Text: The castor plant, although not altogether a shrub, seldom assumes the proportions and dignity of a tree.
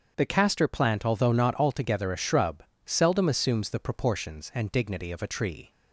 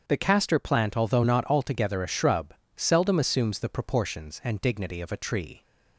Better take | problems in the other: neither | starts louder than the rest; strong; the same in both

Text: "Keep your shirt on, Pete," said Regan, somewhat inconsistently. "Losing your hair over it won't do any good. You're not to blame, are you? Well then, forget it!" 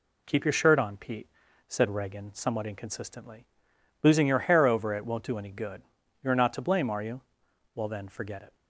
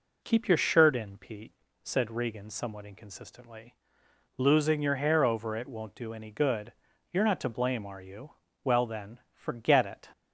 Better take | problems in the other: first | says "in" for "on"; at 0.9 s

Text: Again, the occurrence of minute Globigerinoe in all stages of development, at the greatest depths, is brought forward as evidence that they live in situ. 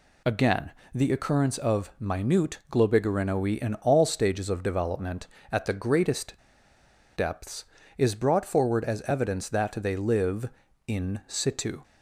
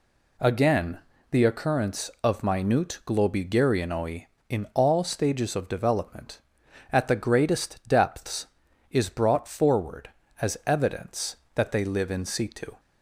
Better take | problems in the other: second | pauses between "greatest" and "depths"; noticeable; at 6.3 s; 0.77 s long

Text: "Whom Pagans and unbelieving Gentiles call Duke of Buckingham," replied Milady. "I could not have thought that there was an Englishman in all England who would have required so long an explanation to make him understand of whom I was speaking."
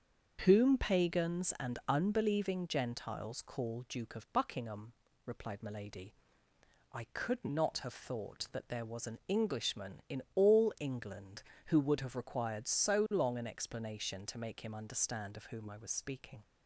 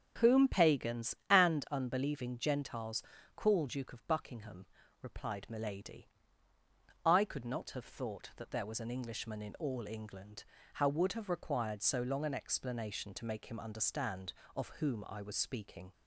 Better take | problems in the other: first | starts louder than the rest; strong; until 1.3 s; 8 dB; also in the first // pauses between "Gentiles" and "call"; slight; at 3.0 s; 0.32 s long // says "how" for "who"; at 10.7 s

